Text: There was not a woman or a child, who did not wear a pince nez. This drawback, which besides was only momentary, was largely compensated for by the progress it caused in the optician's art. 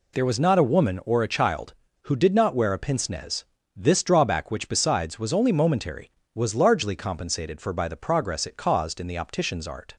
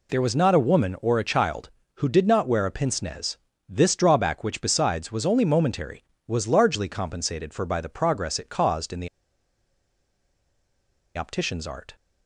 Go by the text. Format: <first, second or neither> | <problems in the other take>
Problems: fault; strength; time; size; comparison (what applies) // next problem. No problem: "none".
first | pauses between "the" and "optician's"; strong; at 9.0 s; 2.0 s long